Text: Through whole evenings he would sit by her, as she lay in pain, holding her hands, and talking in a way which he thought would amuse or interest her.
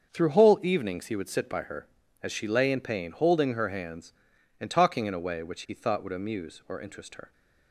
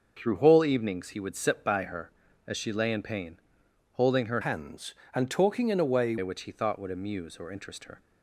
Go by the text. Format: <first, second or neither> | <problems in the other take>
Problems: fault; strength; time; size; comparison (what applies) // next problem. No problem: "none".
first | starts louder than the rest; until 1.1 s; 6 dB; also in the first // changes voice from "hands" to "way"; from 4.4 to 6.1 s; 1.7 s long